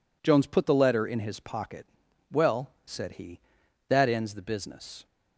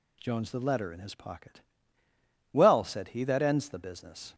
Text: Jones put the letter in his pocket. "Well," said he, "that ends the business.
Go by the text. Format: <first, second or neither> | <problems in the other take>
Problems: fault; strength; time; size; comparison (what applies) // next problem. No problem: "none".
first | skips "put"; at 0.5 s